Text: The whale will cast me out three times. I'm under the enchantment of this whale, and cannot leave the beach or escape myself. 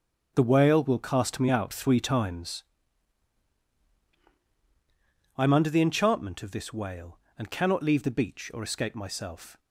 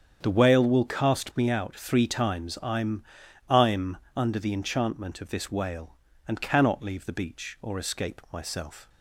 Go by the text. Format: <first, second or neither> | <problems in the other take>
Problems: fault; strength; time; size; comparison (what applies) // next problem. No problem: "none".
first | starts louder than the rest; strong; until 1.2 s; 8 dB; strong in the first // says "I'm" twice; at 3.4 s